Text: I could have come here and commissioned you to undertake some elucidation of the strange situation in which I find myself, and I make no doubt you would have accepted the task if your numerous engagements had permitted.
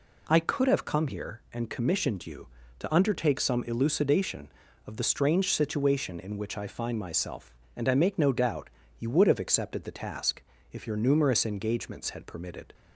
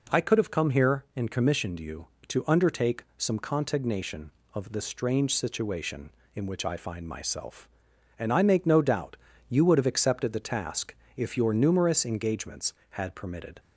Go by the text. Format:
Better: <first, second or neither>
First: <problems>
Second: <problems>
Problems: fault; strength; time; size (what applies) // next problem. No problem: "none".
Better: first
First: pauses between "doubt" and "you"; slight; at 8.6 s; 0.30 s long // pauses between "task" and "if"; slight; at 10.4 s; 0.30 s long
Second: says "contignation" for "elucidation"; at 3.3 s // pauses between "doubt" and "you"; slight; at 9.1 s; 0.32 s long // pauses between "task" and "if"; slight; at 10.9 s; 0.24 s long